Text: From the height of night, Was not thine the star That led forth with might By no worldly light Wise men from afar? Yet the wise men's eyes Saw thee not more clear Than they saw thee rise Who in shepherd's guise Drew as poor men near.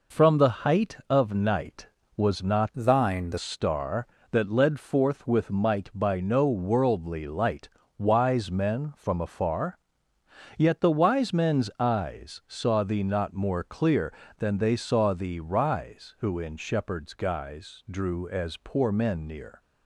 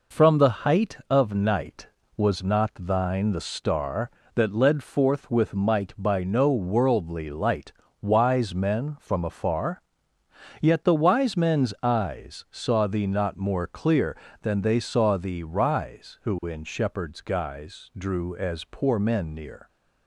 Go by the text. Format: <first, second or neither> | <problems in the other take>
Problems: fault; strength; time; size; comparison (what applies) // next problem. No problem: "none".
second | changes voice from "thine" to "the"; from 2.7 to 3.3 s; 0.6 s long // pauses between "light" and "Wise"; slight; at 7.6 s; 0.30 s long; slight in the second